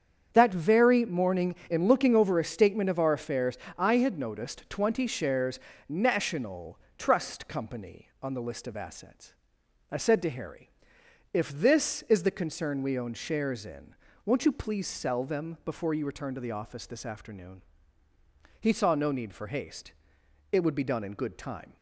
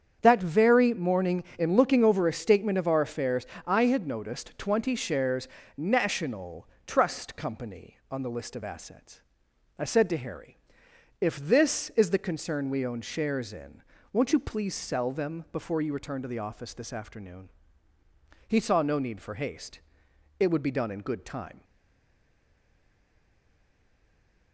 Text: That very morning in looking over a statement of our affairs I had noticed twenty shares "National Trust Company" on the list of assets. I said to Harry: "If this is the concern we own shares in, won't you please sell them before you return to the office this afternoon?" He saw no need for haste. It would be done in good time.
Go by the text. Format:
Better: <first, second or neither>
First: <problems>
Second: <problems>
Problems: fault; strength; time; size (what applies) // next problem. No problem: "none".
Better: first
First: starts louder than the rest; strong; until 1.3 s; 8 dB // pauses between "affairs" and "I"; slight; at 3.5 s; 0.20 s long // pauses between "shares" and "National"; slight; at 5.5 s; 0.28 s long // pauses between "National" and "Trust"; slight; at 6.7 s; 0.20 s long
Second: starts louder than the rest; strong; until 1.2 s; 8 dB // pauses between "affairs" and "I"; slight; at 3.4 s; 0.20 s long // pauses between "shares" and "National"; slight; at 5.4 s; 0.28 s long // pauses between "National" and "Trust"; slight; at 6.6 s; 0.20 s long // stays silent after the last word; strong; from 21.6 s on; 2.9 s long